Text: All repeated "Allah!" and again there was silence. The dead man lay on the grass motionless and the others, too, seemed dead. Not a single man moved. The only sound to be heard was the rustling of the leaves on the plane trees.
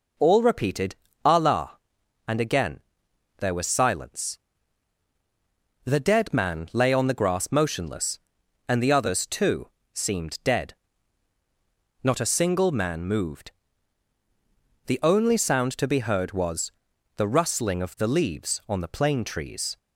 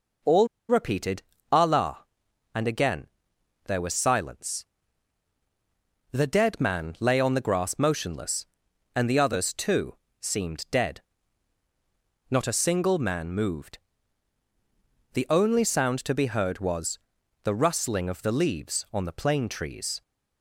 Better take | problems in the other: first | pauses between "All" and "repeated"; slight; at 0.4 s; 0.22 s long // pauses between "repeated" and "Allah"; slight; at 1.2 s; 0.30 s long; slight in the first // pauses between "again" and "there"; noticeable; at 3.0 s; 0.60 s long; noticeable in the first // pauses between "was" and "the"; noticeable; at 16.9 s; 0.46 s long; noticeable in the first

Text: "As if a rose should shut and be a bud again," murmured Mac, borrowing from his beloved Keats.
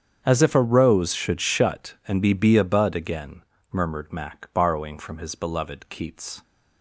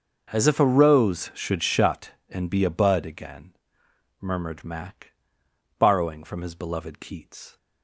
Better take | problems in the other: second | starts louder than the rest; strong; until 1.2 s; 8 dB; noticeable in the second // says "be" twice; at 2.3 s

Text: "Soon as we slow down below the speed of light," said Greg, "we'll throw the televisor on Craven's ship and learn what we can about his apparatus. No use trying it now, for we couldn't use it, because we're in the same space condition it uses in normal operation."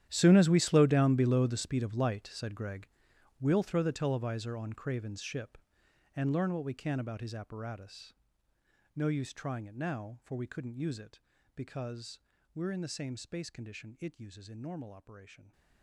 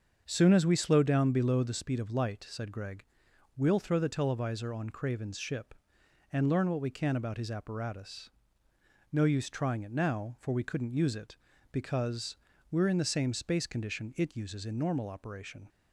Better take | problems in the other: second | gets quieter; strong; throughout; 17.5 dB // starts louder than the rest; strong; until 1.1 s; 11 dB; also in the second // pauses between "because" and "we're"; slight; at 12.1 s; 0.34 s long; slight in the second

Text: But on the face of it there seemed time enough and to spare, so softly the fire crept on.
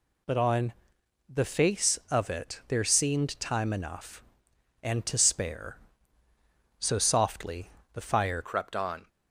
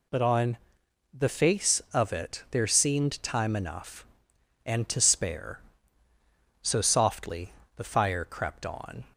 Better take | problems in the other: second | pauses between "on" and "the"; noticeable; at 0.7 s; 0.56 s long; noticeable in the second // pauses between "softly" and "the"; slight; at 7.7 s; 0.24 s long; slight in the second // changes voice at "crept"; from 8.4 s on; 0.6 s long

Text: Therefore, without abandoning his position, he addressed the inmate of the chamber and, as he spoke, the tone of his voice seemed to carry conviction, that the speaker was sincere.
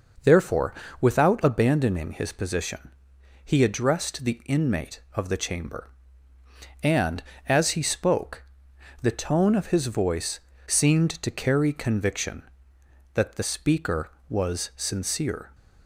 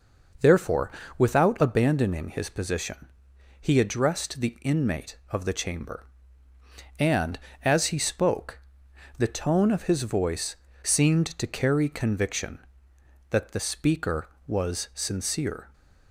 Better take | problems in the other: neither | pauses between "voice" and "seemed"; slight; the same in both

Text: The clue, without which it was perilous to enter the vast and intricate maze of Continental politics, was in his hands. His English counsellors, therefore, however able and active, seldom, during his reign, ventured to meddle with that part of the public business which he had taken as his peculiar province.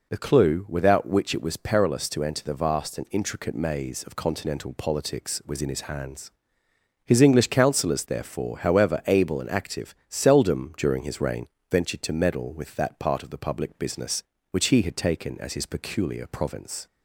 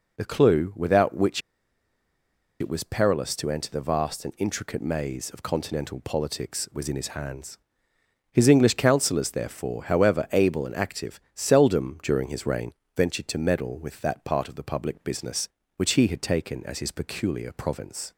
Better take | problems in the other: first | pauses between "which" and "it"; at 1.4 s; 1.2 s long

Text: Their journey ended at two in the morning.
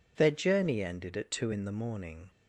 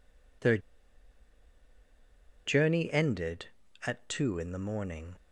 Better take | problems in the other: first | pauses between "Their" and "journey"; strong; at 0.5 s; 1.8 s long

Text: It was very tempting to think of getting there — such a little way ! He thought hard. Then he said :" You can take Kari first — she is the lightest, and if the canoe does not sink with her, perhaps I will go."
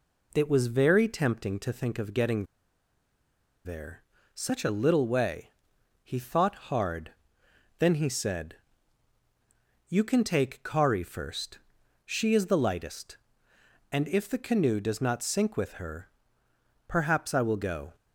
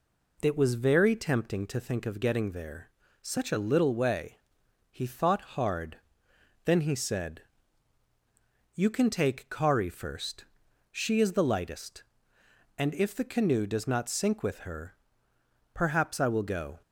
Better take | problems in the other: second | pauses between "getting" and "there"; at 2.4 s; 1.1 s long

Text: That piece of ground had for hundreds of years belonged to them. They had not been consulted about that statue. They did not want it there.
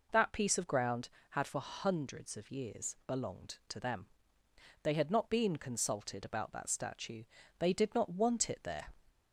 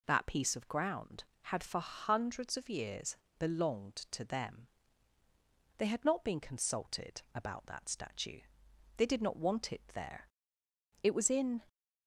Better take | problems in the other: first | pauses between "years" and "belonged"; slight; at 3.1 s; 0.22 s long // goes on to say "It was in"; noticeable; from 11.0 s on; 0.62 s long

